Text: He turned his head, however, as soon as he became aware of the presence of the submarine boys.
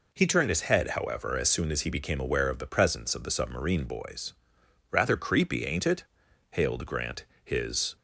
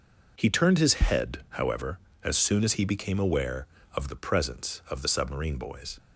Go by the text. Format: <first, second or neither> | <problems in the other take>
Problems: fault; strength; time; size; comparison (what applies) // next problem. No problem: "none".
second | goes on to say "Rather creepy ain't it hailed Grant his"; strong; from 4.8 s on; 3.0 s long